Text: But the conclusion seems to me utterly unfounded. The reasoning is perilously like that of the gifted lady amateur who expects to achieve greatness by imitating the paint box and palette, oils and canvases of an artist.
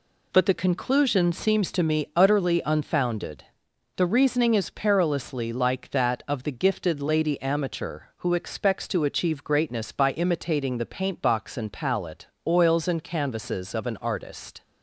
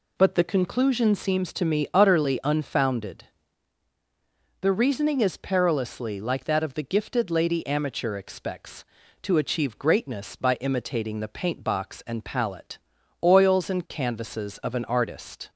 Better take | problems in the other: first | skips "who"; at 8.1 s

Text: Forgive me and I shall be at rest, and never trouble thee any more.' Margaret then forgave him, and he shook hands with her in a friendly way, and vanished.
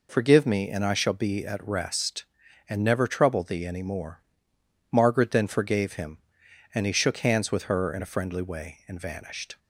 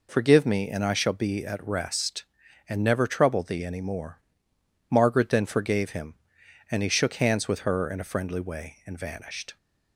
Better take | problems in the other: neither | none

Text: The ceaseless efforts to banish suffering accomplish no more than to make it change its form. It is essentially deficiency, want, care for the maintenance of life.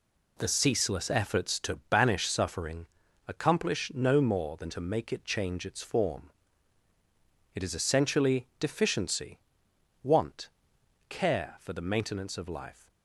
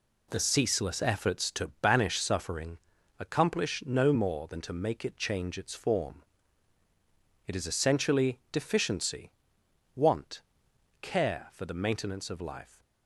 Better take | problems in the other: neither | pauses between "suffering" and "accomplish"; the same in both

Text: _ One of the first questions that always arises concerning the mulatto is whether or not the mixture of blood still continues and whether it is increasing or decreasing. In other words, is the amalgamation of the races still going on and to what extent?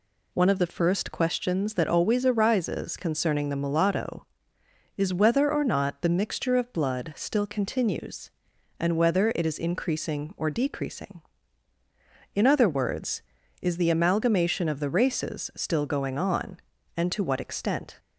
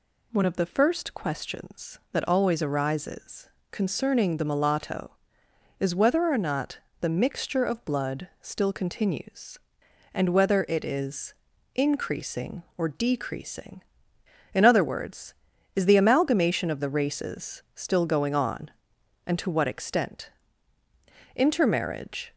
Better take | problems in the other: first | pauses between "arises" and "concerning"; slight; at 3.4 s; 0.24 s long // pauses between "not" and "the"; slight; at 6.7 s; 0.20 s long // pauses between "is" and "increasing"; at 11.3 s; 0.42 s long // goes on to say "Intermarriage"; noticeable; from 21.3 s on; 0.96 s long

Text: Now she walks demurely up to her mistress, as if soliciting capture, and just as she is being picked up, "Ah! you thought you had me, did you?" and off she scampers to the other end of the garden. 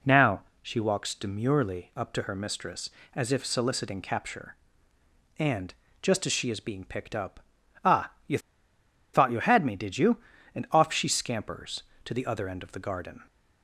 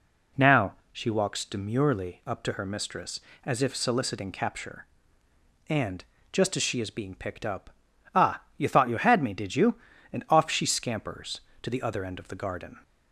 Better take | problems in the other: second | pauses between "Now" and "she"; slight; at 0.4 s; 0.20 s long; slight in the second // pauses between "and" and "just"; slight; at 5.7 s; 0.28 s long; slight in the second // pauses between "you" and "thought"; noticeable; at 8.3 s; 0.75 s long

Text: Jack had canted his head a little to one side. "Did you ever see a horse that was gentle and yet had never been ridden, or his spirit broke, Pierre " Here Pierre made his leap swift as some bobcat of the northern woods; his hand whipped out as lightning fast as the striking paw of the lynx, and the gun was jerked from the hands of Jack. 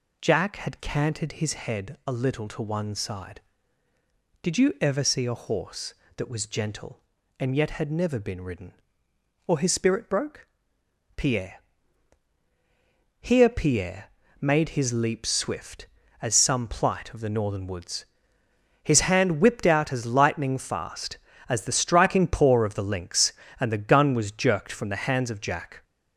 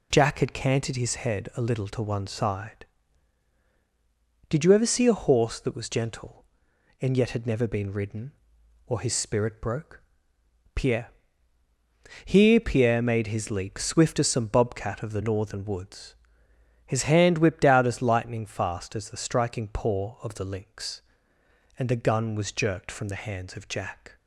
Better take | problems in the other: second | pauses between "Pierre" and "made"; slight; at 14.0 s; 0.36 s long // says "plight" for "bobcat"; at 16.6 s

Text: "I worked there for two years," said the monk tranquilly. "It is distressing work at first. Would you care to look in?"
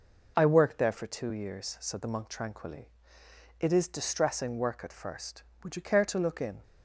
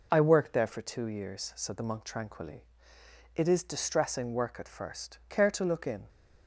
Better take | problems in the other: first | skips "Would you"; at 5.2 s

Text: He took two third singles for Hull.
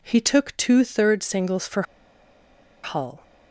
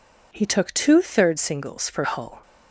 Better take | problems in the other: second | pauses between "for" and "Hull"; at 1.8 s; 1.0 s long

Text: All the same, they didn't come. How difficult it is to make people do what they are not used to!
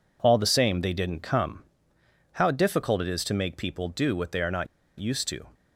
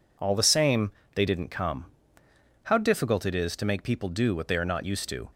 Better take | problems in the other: second | pauses between "not" and "used"; slight; at 4.6 s; 0.31 s long

